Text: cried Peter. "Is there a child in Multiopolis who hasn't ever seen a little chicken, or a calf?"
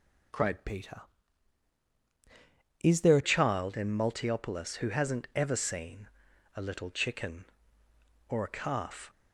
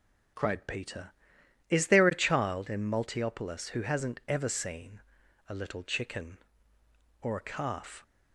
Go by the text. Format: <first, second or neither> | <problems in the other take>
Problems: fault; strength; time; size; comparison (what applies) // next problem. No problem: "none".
second | changes voice from "Peter" to "a"; from 0.6 to 3.2 s; 2.6 s long // pauses between "seen" and "a"; noticeable; at 6.0 s; 0.46 s long; noticeable in the second